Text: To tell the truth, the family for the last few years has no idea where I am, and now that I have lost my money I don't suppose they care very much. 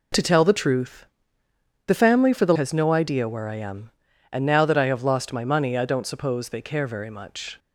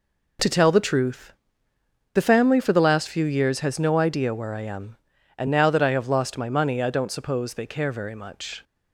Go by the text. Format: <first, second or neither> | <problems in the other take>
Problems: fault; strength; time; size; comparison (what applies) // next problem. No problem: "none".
second | skips "last few years"; at 2.5 s